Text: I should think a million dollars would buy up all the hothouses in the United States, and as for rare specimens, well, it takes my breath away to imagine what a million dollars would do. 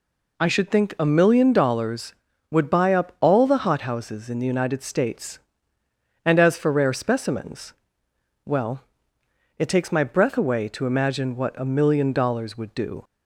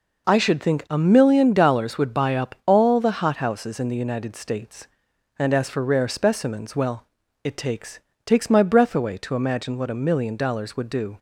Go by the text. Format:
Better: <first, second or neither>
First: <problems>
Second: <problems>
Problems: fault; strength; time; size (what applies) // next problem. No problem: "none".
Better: first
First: none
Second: says "takes" twice; at 8.2 s